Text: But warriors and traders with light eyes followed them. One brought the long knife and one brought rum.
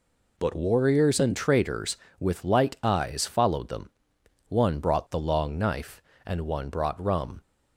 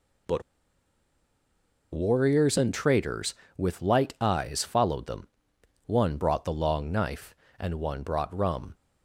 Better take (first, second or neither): first